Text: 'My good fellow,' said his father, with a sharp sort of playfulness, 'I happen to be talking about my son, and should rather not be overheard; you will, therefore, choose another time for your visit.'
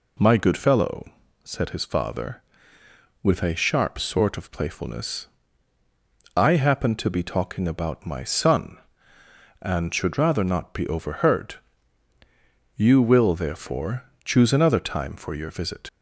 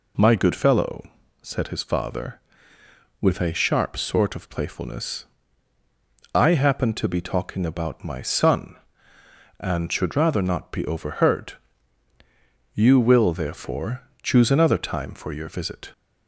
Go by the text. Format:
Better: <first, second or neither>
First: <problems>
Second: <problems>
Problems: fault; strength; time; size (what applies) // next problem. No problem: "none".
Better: second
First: leaves "visit" unfinished; at 15.8 s; 50 ms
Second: none